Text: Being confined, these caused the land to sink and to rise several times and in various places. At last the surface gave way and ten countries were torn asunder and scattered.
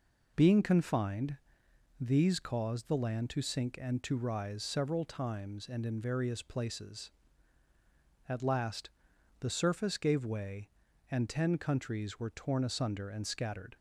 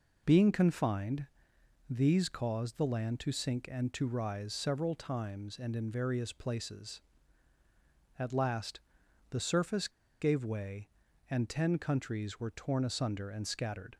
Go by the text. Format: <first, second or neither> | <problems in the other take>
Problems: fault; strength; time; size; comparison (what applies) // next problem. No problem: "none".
first | pauses between "last" and "the"; noticeable; at 8.7 s; 0.52 s long; noticeable in the first // pauses between "surface" and "gave"; slight; at 9.8 s; 0.32 s long